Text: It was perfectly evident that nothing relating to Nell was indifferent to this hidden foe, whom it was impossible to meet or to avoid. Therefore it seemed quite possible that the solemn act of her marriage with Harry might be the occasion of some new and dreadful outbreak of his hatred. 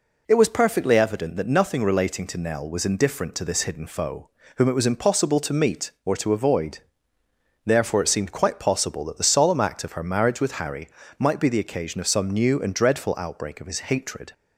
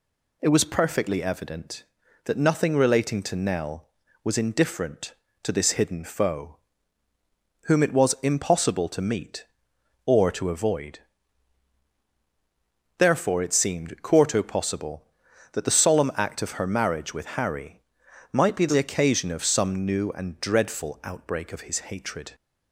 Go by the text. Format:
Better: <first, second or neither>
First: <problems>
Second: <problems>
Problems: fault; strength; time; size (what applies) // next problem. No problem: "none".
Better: first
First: pauses between "Harry" and "might"; slight; at 10.8 s; 0.32 s long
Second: says "quarto" for "quite"; at 14.0 s // pauses between "Harry" and "might"; noticeable; at 17.7 s; 0.52 s long